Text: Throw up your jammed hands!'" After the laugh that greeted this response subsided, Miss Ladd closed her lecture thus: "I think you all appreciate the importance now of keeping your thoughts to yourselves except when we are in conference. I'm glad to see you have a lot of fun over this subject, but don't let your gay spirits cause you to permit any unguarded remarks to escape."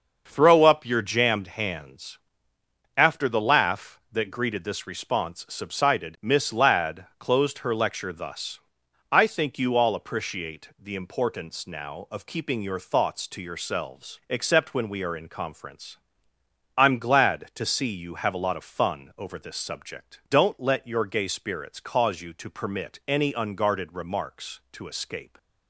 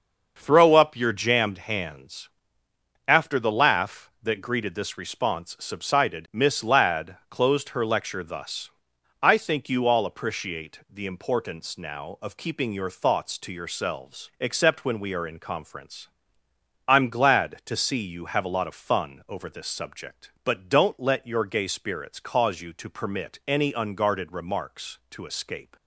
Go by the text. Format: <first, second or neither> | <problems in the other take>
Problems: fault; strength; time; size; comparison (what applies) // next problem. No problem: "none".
second | starts louder than the rest; until 1.2 s; 6 dB; also in the second // skips "but"; at 20.2 s